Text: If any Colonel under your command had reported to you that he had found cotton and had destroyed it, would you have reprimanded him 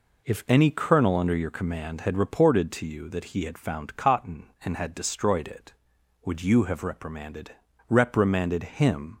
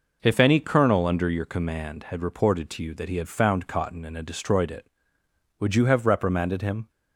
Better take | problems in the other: second | says "reprimanded" twice; at 7.8 s

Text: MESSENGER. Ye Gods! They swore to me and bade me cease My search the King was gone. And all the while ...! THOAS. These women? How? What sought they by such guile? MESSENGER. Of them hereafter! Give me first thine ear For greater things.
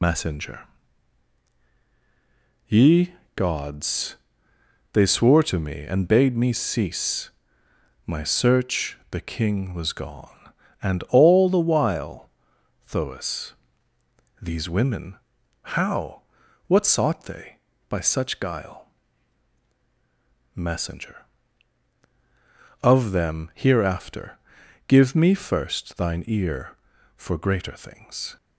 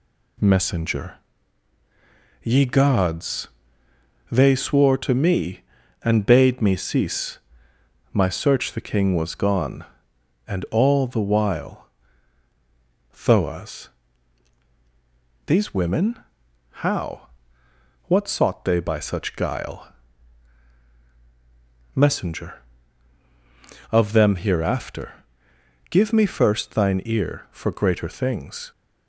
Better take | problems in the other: second | loses the start of "MESSENGER"; at 0.0 s; 105 ms // pauses between "Ye" and "Gods"; slight; at 3.1 s; 0.22 s long // pauses between "cease" and "My"; noticeable; at 7.3 s; 0.76 s long; noticeable in the second

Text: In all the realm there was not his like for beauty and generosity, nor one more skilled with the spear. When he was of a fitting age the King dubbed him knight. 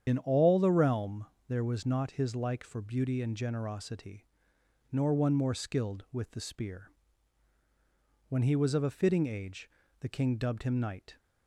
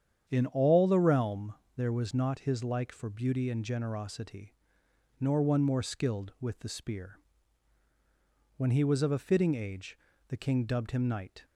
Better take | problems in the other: second | loses the start of "In"; at 0.0 s; 65 ms // starts louder than the rest; strong; until 1.0 s; 8.5 dB; strong in the second // pauses between "realm" and "there"; slight; at 1.2 s; 0.22 s long; slight in the second // pauses between "age" and "the"; slight; at 9.6 s; 0.30 s long; slight in the second

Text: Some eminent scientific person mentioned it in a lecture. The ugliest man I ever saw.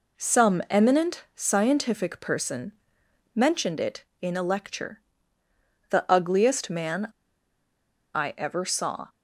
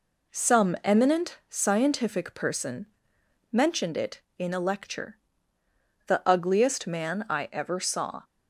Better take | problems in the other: second | pauses between "person" and "mentioned"; noticeable; at 2.7 s; 0.62 s long; noticeable in the second // pauses between "man" and "I"; at 7.0 s; 1.0 s long

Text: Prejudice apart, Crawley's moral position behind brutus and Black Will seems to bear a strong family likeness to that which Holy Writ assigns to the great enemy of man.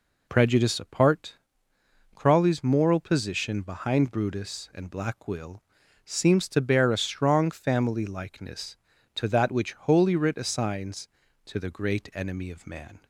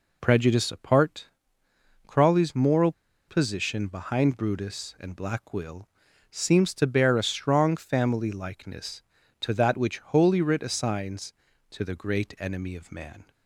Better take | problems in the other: first | pauses between "moral" and "position"; slight; at 2.9 s; 0.35 s long // pauses between "Will" and "seems"; at 5.8 s; 0.42 s long; also in the first

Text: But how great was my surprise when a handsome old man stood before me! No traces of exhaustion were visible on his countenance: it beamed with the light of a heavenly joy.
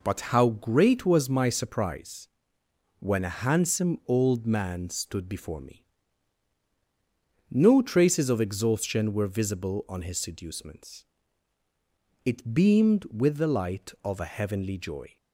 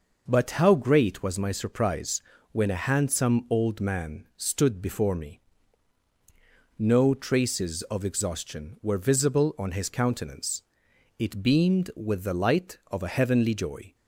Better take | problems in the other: second | pauses between "surprise" and "when"; noticeable; at 2.2 s; 0.72 s long; slight in the second // says "seducements" for "countenance"; at 10.1 s

